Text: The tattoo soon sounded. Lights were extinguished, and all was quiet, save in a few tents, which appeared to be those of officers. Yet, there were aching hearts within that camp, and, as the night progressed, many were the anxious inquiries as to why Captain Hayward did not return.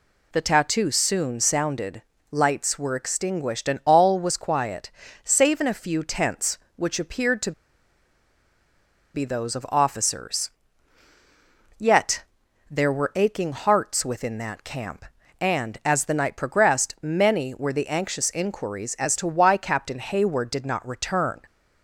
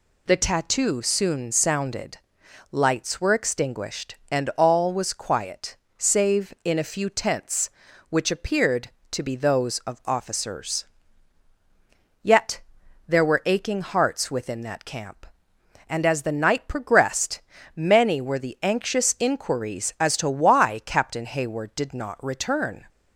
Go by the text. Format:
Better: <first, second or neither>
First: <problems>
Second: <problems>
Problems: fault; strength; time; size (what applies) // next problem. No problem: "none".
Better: second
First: pauses between "to" and "be"; strong; at 7.5 s; 1.6 s long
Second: none